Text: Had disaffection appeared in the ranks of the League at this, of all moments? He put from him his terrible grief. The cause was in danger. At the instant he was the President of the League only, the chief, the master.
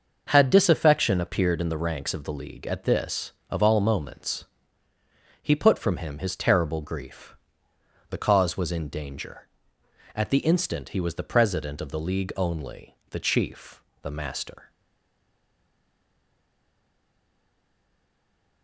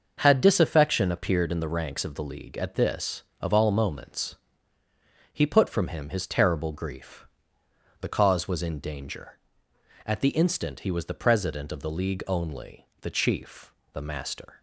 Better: second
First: starts louder than the rest; noticeable; until 1.2 s; 6 dB // stays silent after the last word; strong; from 14.6 s on; 4.0 s long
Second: starts louder than the rest; noticeable; until 1.1 s; 6 dB

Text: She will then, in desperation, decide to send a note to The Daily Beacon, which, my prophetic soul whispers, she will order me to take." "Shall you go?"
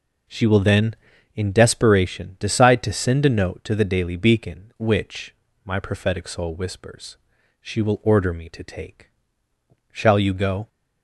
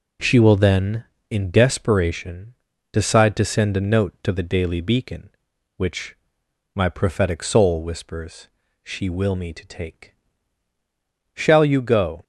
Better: first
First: none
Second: skips "order"; at 9.3 s

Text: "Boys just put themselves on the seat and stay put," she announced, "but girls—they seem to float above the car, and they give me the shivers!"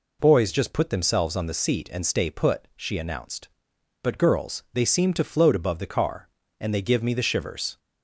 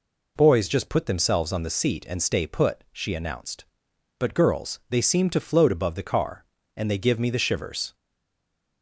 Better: first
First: none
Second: stays silent after the last word; slight; from 7.9 s on; 0.9 s long

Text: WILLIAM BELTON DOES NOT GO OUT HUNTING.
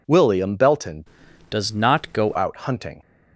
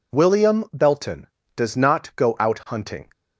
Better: second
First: changes voice from "DOES" to "GO"; from 1.5 to 2.3 s; 0.8 s long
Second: none

